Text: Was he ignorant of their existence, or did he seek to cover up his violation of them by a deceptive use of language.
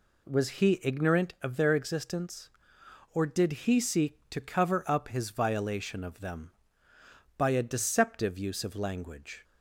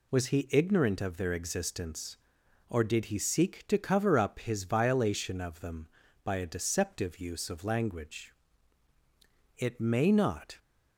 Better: first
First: none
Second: goes on to say "It may not"; noticeable; from 9.5 s on; 1.0 s long

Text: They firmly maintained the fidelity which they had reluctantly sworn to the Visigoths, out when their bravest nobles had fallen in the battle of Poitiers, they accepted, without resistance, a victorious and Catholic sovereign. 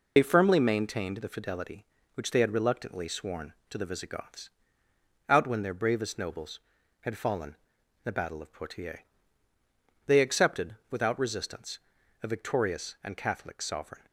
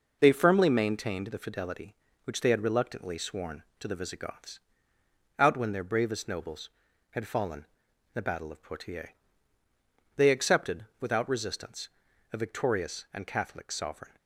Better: second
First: loses the start of "They"; at 0.1 s; 45 ms // pauses between "in" and "the"; noticeable; at 7.5 s; 0.48 s long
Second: pauses between "in" and "the"; noticeable; at 7.6 s; 0.48 s long

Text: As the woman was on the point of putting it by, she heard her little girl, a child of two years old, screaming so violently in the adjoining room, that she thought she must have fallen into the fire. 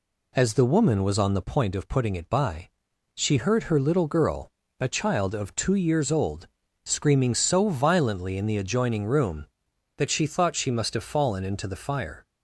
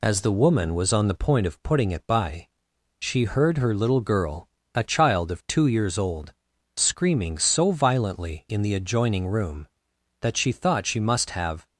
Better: first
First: none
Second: stops before "fallen into the fire"; at 11.6 s

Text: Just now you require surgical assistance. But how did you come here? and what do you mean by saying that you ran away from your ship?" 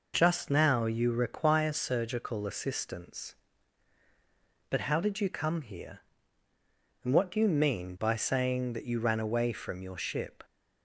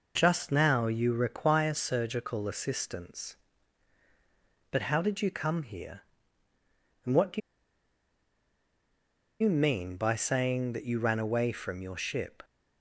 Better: first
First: none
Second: pauses between "do" and "you"; strong; at 7.4 s; 2.0 s long

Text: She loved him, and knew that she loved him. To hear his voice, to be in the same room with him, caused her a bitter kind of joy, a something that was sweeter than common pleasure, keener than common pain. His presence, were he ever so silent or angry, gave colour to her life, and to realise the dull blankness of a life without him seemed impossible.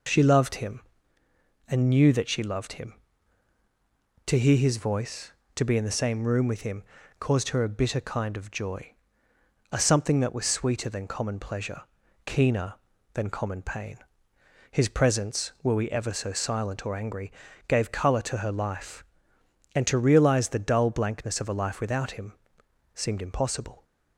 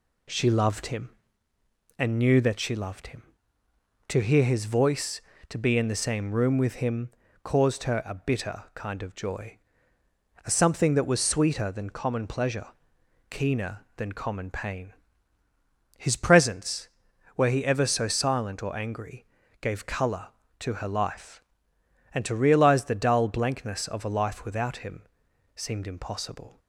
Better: second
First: says "we" for "he"; at 15.7 s // pauses between "him" and "seemed"; noticeable; at 22.3 s; 0.64 s long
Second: pauses between "him" and "seemed"; noticeable; at 25.0 s; 0.54 s long

